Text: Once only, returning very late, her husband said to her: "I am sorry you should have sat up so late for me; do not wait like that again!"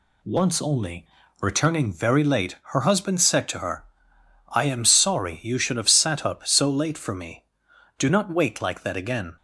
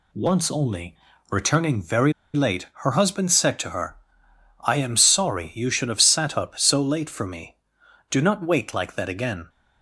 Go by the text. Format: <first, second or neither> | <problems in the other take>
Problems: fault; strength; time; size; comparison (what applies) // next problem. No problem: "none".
first | pauses between "very" and "late"; slight; at 2.1 s; 0.22 s long